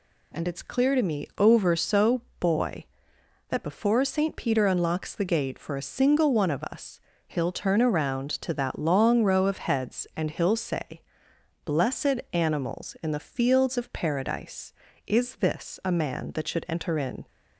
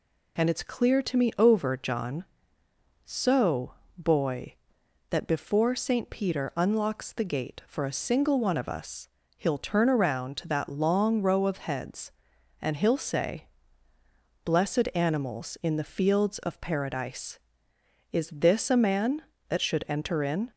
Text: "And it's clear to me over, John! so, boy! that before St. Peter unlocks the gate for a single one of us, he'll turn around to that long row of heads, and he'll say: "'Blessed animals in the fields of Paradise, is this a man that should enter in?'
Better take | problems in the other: second | skips "John"; at 1.7 s

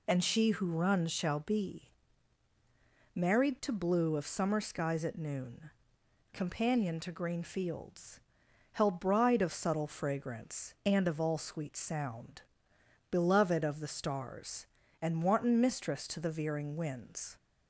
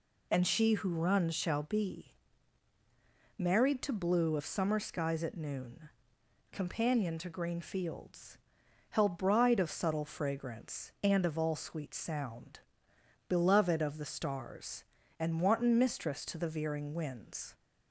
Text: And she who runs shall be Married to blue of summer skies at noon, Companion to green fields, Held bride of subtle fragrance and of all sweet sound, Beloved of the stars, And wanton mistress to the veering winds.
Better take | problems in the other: neither | pauses between "be" and "Married"; the same in both

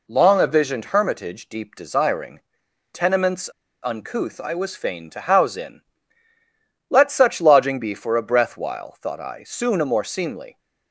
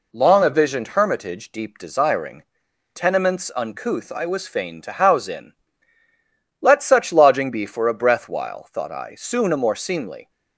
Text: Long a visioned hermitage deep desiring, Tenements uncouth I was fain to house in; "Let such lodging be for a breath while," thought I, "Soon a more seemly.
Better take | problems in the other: second | pauses between "Tenements" and "uncouth"; slight; at 3.5 s; 0.32 s long

